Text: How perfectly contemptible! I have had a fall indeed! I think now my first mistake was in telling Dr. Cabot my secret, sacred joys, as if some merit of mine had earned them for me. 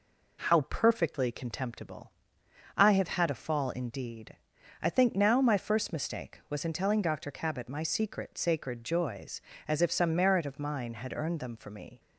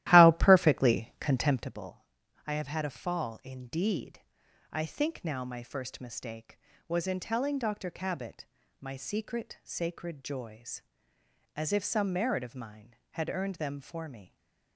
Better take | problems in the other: first | starts louder than the rest; strong; until 1.8 s; 14.5 dB // pauses between "Cabot" and "my"; slight; at 8.4 s; 0.34 s long // stays silent after the last word; slight; from 14.2 s on; 0.5 s long

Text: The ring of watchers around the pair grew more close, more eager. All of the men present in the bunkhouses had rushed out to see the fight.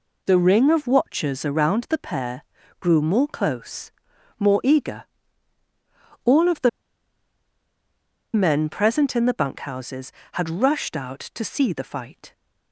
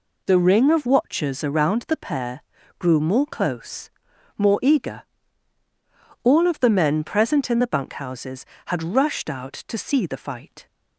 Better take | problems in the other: second | pauses between "pair" and "grew"; slight; at 2.4 s; 0.34 s long; slight in the second // pauses between "the" and "men"; strong; at 6.6 s; 1.6 s long

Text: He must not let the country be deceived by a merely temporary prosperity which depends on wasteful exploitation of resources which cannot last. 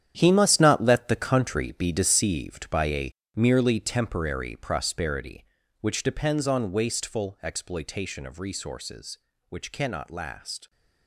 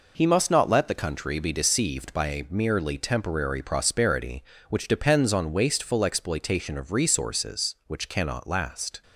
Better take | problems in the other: second | gets quieter; strong; throughout; 12 dB // pauses between "a" and "merely"; slight; at 3.1 s; 0.24 s long

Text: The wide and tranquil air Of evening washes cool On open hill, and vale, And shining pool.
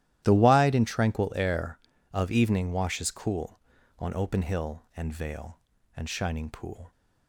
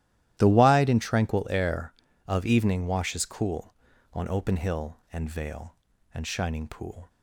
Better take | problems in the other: neither | starts louder than the rest; strong; the same in both

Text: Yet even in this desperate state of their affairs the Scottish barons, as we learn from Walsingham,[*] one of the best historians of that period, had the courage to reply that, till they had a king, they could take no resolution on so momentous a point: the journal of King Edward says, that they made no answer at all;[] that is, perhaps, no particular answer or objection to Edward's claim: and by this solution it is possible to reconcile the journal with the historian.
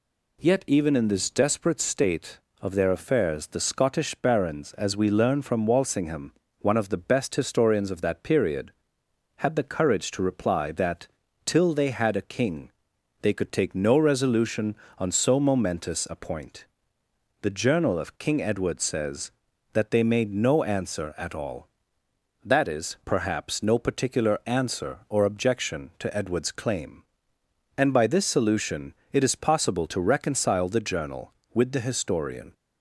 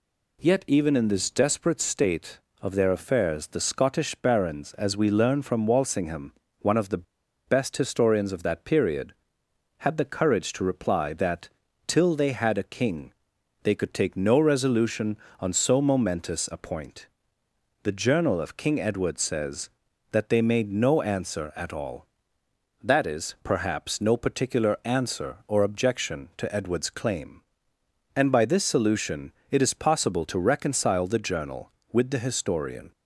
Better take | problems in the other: first | pauses between "the" and "best"; at 7.0 s; 0.42 s long // pauses between "solution" and "it"; slight; at 29.3 s; 0.18 s long; slight in the first

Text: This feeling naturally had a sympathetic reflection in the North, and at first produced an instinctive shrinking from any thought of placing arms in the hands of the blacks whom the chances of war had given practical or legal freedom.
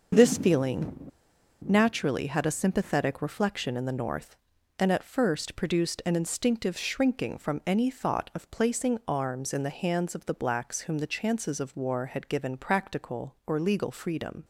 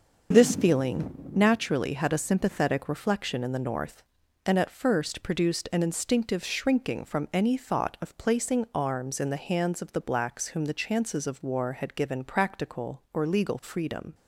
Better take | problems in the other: second | pauses between "feeling" and "naturally"; noticeable; at 1.1 s; 0.58 s long

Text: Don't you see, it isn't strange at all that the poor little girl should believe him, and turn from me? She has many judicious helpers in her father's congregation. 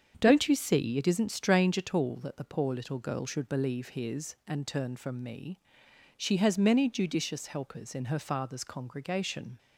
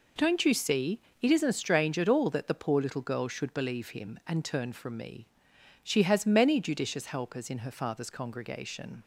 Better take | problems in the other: second | starts louder than the rest; strong; until 1.2 s; 7.5 dB // says "his" for "him"; at 3.8 s

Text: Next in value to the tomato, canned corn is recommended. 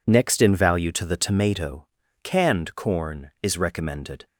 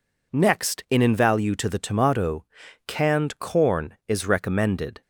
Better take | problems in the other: first | says "in" twice; at 1.0 s

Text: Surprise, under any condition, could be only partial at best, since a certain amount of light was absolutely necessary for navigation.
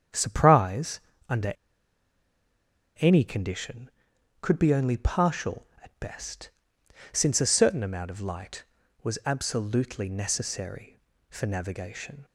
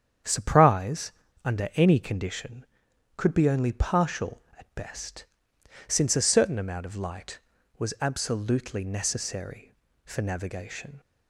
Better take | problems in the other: second | starts louder than the rest; strong; until 1.4 s; 8.5 dB; strong in the second // pauses between "under" and "any"; strong; at 1.5 s; 1.4 s long

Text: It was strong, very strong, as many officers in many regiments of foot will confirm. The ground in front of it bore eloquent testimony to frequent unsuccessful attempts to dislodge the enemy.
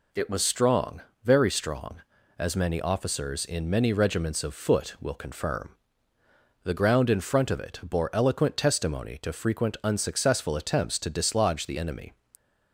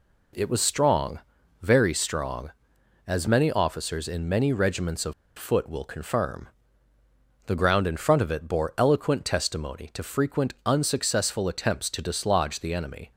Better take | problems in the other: first | pauses between "of" and "foot"; slight; at 5.1 s; 0.23 s long

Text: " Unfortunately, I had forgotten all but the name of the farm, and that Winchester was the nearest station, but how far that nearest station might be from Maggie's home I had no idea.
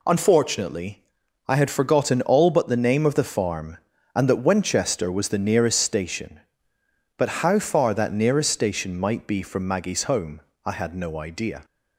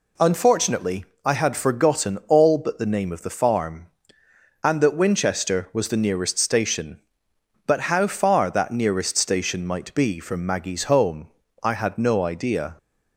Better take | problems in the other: neither | pauses between "home" and "I"; slight; the same in both

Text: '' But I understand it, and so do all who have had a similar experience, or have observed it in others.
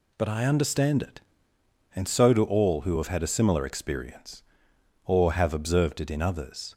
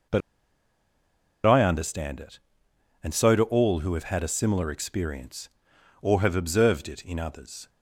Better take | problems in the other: first | pauses between "But" and "I"; strong; at 0.2 s; 1.2 s long

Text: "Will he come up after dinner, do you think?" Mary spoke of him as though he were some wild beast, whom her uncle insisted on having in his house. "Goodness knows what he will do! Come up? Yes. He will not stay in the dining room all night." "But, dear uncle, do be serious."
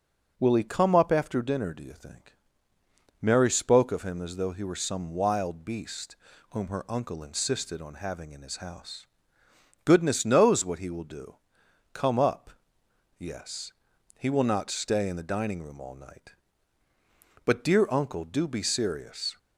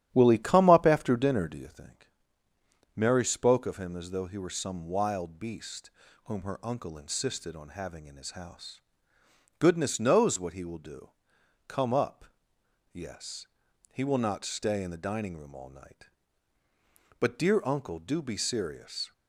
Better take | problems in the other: first | starts louder than the rest; strong; until 1.9 s; 11 dB

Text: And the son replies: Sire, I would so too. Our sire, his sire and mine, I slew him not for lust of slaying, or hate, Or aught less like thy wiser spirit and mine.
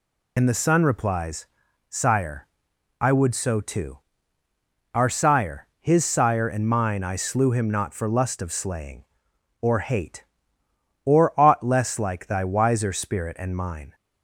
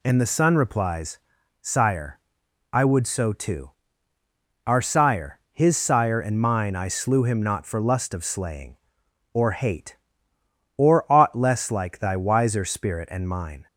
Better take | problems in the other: second | loses the start of "And"; at 0.3 s; 60 ms

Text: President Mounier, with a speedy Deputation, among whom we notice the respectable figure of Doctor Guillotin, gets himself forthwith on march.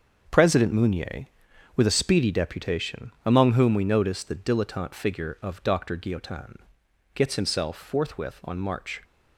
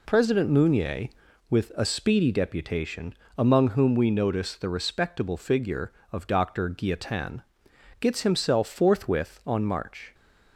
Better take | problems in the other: second | starts louder than the rest; until 1.8 s; 7 dB // says "dilettante" for "respectable"; at 4.3 s

